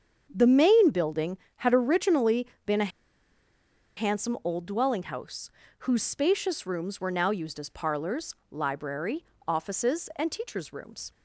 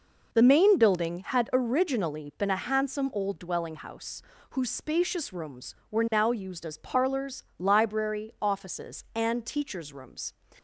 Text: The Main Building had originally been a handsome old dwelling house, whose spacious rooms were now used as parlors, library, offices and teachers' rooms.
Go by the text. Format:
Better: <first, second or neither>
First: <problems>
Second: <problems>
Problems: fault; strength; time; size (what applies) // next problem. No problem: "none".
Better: second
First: starts louder than the rest; strong; until 1.3 s; 7.5 dB // pauses between "originally" and "been"; slight; at 2.4 s; 0.20 s long // pauses between "a" and "handsome"; at 2.9 s; 1.0 s long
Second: none